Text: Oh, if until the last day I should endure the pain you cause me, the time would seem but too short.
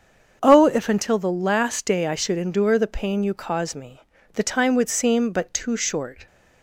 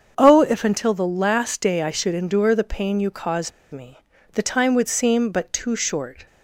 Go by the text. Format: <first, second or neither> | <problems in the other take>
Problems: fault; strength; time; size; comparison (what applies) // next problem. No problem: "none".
first | starts louder than the rest; until 1.1 s; 7 dB; also in the first // pauses between "cause" and "me"; slight; at 3.5 s; 0.20 s long